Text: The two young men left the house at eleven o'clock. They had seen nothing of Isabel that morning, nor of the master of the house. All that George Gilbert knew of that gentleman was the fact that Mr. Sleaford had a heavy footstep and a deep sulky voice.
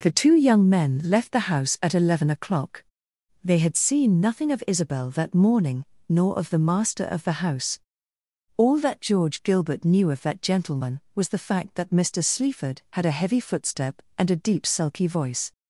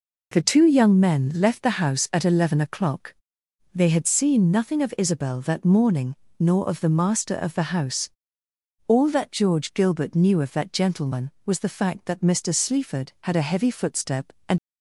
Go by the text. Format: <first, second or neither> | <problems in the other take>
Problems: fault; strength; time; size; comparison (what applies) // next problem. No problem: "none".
first | stops before "a deep sulky voice"; at 14.5 s